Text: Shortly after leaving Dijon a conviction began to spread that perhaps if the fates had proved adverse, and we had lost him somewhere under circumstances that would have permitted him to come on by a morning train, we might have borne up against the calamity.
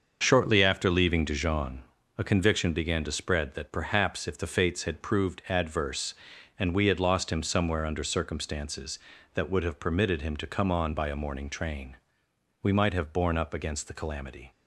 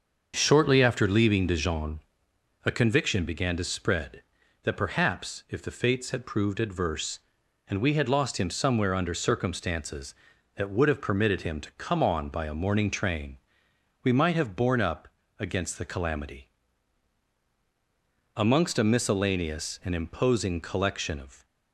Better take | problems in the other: first | starts louder than the rest; until 1.3 s; 6.5 dB; also in the first // pauses between "Dijon" and "a"; noticeable; at 2.0 s; 0.64 s long; also in the first // pauses between "up" and "against"; slight; at 15.0 s; 0.32 s long // goes on to say "Amongst a miscellaneous and imposing collection of"; strong; from 18.3 s on; 3.1 s long

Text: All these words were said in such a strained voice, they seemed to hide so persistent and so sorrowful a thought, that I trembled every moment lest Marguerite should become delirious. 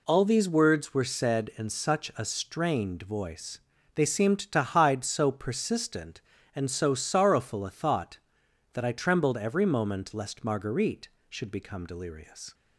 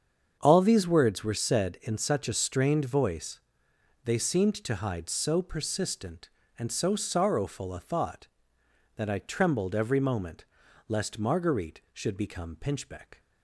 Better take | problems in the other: first | starts louder than the rest; strong; until 1.4 s; 7 dB // pauses between "moment" and "lest"; at 10.4 s; 0.44 s long // says "pinchbeck" for "delirious"; at 12.5 s

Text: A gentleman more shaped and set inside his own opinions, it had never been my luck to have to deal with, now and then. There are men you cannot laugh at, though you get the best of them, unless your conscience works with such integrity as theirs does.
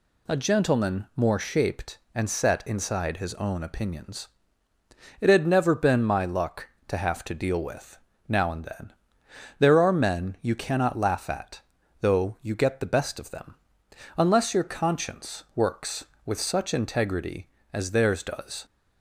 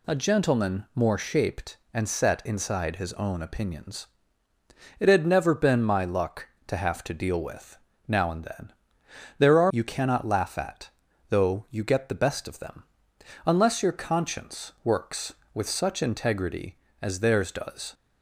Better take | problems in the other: first | skips "men"; at 9.7 s

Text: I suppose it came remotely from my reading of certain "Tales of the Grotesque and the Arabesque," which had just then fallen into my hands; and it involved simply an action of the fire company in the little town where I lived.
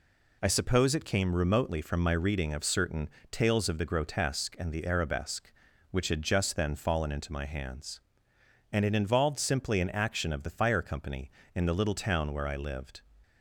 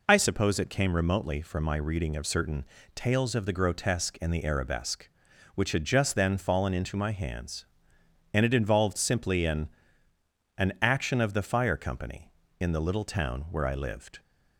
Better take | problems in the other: first | pauses between "certain" and "Tales"; slight; at 2.6 s; 0.28 s long; slight in the first // says "an" twice; at 10.5 s

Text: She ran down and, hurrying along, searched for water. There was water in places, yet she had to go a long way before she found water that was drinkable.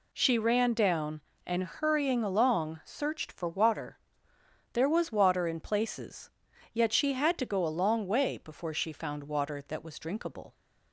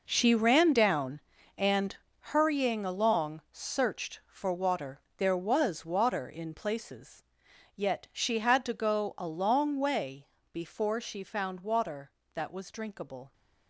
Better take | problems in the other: first | gets quieter; strong; throughout; 13 dB // pauses between "way" and "before"; slight; at 10.2 s; 0.24 s long

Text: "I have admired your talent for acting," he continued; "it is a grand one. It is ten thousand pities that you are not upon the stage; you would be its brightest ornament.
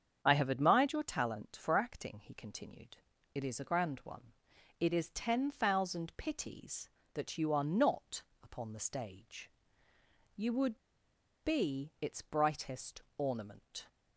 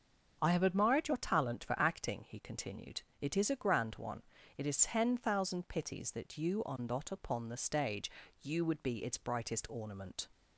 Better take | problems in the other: second | starts louder than the rest; strong; until 1.2 s; 7.5 dB; also in the second // pauses between "not" and "upon"; slight; at 8.2 s; 0.18 s long // pauses between "would" and "be"; noticeable; at 10.7 s; 0.64 s long // pauses between "brightest" and "ornament"; slight; at 13.0 s; 0.16 s long

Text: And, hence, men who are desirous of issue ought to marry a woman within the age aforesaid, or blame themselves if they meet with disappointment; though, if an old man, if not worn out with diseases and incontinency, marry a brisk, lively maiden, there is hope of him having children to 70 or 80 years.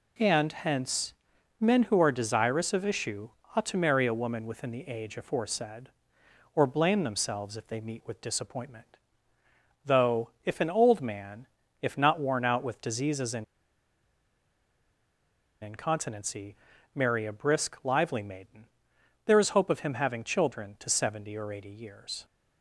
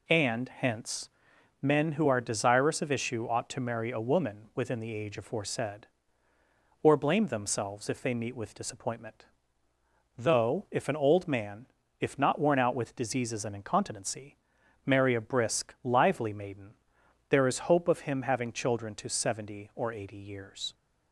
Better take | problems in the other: second | pauses between "issue" and "ought"; slight; at 3.2 s; 0.24 s long // pauses between "and" and "incontinency"; strong; at 13.4 s; 2.1 s long

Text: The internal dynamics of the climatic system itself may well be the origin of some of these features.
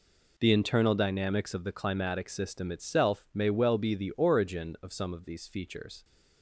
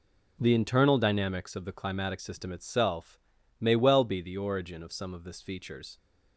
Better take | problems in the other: first | pauses between "itself" and "may"; at 3.1 s; 0.42 s long // says "this" for "these"; at 5.2 s

